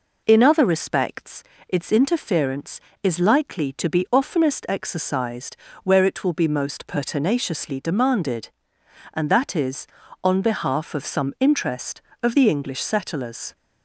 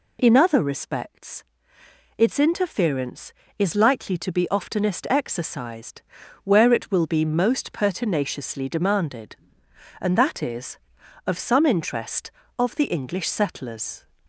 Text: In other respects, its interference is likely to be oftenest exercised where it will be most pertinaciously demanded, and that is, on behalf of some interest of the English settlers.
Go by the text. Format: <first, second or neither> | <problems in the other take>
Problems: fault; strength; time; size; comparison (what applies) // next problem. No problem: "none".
first | pauses between "exercised" and "where"; at 6.0 s; 0.42 s long; slight in the first // skips "on behalf"; at 11.0 s